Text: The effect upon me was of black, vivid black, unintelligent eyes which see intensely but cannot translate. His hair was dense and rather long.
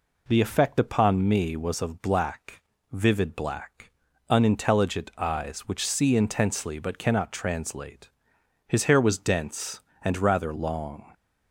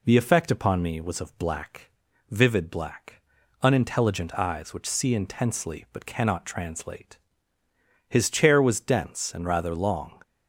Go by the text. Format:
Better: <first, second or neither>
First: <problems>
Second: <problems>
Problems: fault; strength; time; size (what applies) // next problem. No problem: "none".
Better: first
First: none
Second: says "chair" for "hair"; at 8.2 s